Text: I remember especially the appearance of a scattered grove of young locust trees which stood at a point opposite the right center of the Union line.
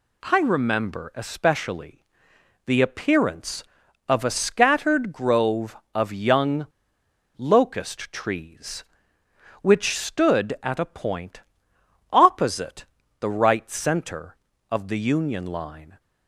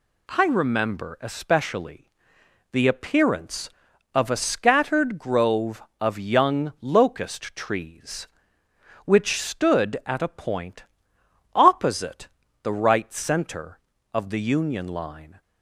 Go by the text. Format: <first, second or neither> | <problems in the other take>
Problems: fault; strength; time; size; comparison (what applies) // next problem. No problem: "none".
second | pauses between "especially" and "the"; noticeable; at 2.0 s; 0.60 s long; noticeable in the second // pauses between "young" and "locust"; noticeable; at 6.6 s; 0.70 s long // pauses between "point" and "opposite"; noticeable; at 11.4 s; 0.68 s long; noticeable in the second // pauses between "opposite" and "the"; slight; at 12.8 s; 0.34 s long; slight in the second